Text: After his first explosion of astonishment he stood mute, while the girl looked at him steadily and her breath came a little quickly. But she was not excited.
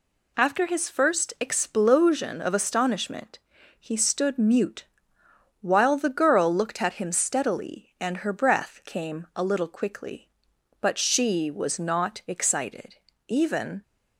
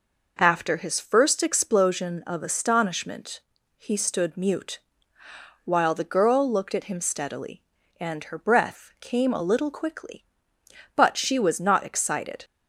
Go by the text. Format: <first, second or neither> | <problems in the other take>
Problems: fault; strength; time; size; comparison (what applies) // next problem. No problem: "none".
second | pauses between "astonishment" and "he"; at 3.3 s; 0.40 s long; also in the second // goes on to say "Even"; from 13.2 s on; 0.54 s long